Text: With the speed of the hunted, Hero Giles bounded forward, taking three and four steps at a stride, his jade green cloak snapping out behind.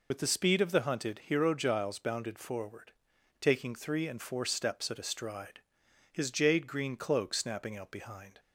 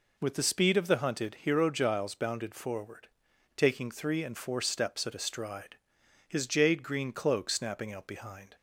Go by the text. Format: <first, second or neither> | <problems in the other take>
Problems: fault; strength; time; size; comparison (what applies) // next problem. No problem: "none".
second | loses the start of "With"; at 0.1 s; 70 ms